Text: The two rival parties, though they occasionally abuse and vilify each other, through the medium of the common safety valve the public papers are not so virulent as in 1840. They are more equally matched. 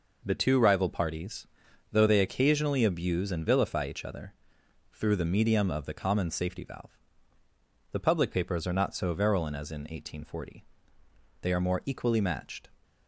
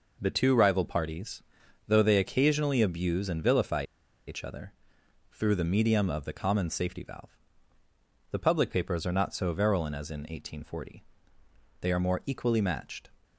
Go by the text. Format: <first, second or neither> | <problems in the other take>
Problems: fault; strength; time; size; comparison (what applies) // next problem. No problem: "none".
first | pauses between "vilify" and "each"; at 3.8 s; 0.42 s long // pauses between "valve" and "the"; noticeable; at 7.3 s; 0.98 s long; noticeable in the first